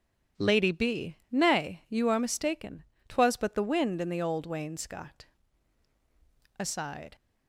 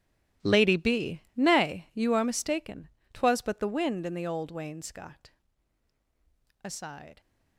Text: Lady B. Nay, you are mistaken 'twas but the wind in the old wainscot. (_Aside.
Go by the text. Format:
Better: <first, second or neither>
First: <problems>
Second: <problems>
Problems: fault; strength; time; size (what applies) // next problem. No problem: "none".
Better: first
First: starts louder than the rest; strong; until 1.5 s; 8.5 dB // pauses between "mistaken" and "twas"; slight; at 2.8 s; 0.24 s long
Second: gets quieter; strong; throughout; 16 dB // starts louder than the rest; strong; until 1.5 s; 13.5 dB // pauses between "mistaken" and "twas"; slight; at 2.8 s; 0.24 s long